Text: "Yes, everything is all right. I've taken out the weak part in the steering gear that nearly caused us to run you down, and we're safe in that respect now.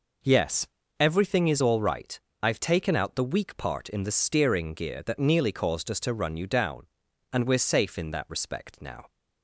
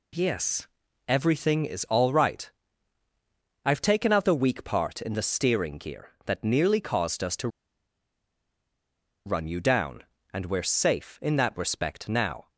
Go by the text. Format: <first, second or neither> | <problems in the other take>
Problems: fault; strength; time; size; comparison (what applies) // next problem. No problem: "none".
first | pauses between "to" and "run"; strong; at 7.4 s; 1.7 s long